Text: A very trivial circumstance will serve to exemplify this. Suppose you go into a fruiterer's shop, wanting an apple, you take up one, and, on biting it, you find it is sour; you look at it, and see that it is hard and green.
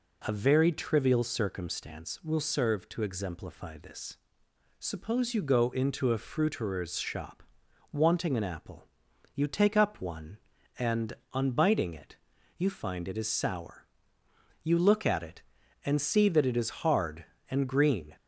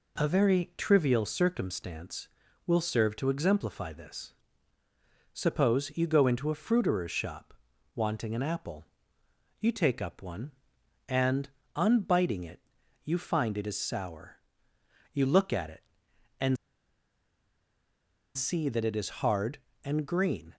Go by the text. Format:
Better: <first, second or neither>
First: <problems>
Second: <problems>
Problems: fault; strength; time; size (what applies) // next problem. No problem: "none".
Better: first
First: none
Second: pauses between "and" and "see"; strong; at 16.5 s; 1.7 s long